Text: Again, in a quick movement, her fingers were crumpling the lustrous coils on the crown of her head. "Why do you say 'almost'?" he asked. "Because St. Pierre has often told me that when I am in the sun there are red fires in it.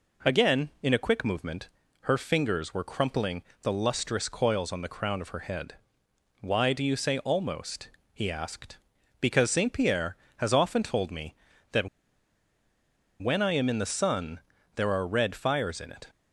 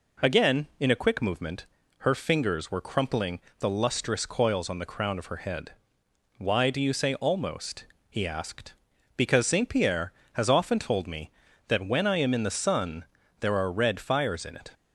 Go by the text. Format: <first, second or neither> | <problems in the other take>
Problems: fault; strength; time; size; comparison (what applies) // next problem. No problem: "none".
second | pauses between "crumpling" and "the"; slight; at 3.4 s; 0.22 s long; slight in the second // pauses between "that" and "when"; strong; at 11.8 s; 1.3 s long // pauses between "sun" and "there"; slight; at 14.4 s; 0.36 s long; slight in the second